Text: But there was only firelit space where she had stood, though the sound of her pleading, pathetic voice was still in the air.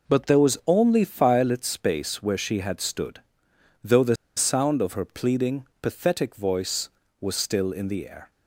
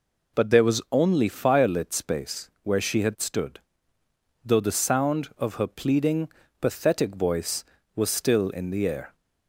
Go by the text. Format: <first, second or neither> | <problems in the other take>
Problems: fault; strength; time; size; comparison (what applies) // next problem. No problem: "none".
second | pauses between "the" and "sound"; slight; at 4.1 s; 0.21 s long